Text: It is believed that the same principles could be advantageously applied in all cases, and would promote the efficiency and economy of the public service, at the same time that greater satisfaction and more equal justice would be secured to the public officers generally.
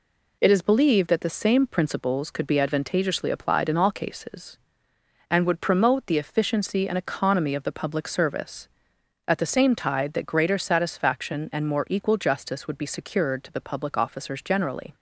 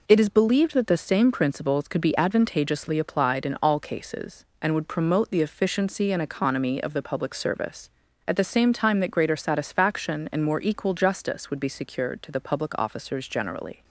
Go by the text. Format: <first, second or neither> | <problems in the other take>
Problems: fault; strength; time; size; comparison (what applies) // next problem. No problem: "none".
second | says "tide" for "time"; at 9.7 s